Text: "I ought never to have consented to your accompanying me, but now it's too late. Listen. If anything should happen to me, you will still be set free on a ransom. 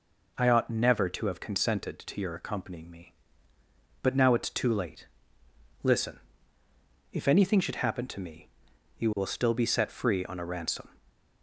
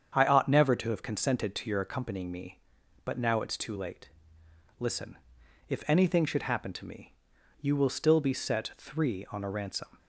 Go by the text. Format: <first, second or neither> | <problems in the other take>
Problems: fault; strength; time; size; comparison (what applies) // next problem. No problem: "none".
first | starts louder than the rest; strong; until 1.1 s; 7.5 dB // says "three" for "free"; at 8.7 s